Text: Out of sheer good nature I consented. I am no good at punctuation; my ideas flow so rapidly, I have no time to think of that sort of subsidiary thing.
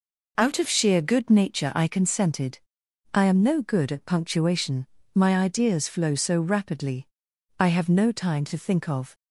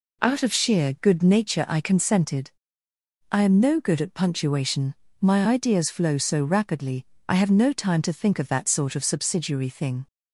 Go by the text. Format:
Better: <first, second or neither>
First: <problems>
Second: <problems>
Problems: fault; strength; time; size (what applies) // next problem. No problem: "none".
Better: second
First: stops before "that sort of subsidiary thing"; at 9.1 s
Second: none